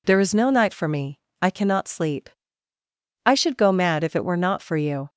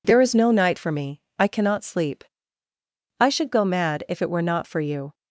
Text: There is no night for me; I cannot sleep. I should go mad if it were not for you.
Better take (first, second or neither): neither